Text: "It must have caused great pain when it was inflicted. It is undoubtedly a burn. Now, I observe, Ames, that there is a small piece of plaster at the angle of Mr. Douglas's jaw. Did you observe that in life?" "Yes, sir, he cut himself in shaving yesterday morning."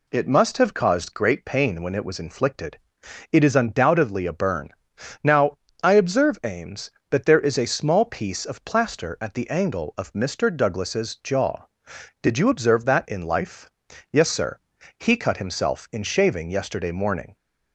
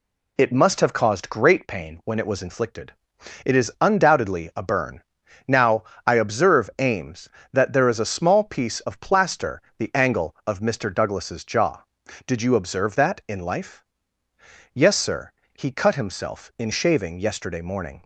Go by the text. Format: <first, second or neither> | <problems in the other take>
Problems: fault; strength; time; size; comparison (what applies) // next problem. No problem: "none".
first | skips "at"; at 9.7 s